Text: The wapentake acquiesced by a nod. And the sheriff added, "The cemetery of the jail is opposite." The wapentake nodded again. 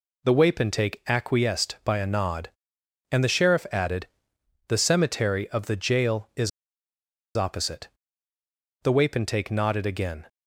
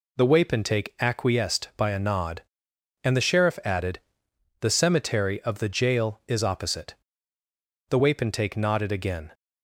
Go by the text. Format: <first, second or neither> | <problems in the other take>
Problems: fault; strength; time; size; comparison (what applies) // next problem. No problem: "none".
second | pauses between "is" and "opposite"; noticeable; at 6.4 s; 0.87 s long